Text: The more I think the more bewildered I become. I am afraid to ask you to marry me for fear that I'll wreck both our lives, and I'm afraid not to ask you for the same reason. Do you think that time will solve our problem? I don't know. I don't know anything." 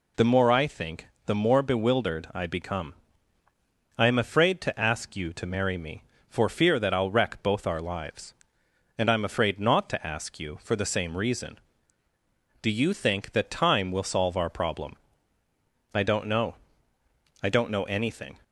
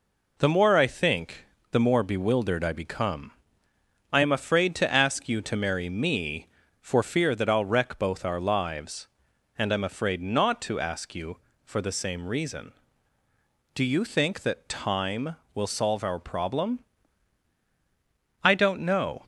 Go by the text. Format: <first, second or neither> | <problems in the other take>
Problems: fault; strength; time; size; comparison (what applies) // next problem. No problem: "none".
first | pauses between "think" and "the"; slight; at 1.4 s; 0.26 s long; slight in the first // stops before "I don't know anything"; at 19.2 s